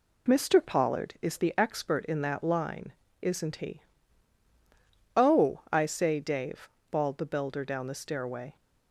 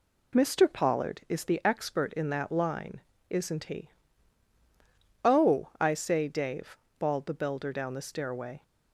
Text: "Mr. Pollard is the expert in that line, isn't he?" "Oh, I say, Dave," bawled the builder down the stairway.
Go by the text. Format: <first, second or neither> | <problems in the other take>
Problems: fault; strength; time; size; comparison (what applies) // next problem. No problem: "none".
neither | none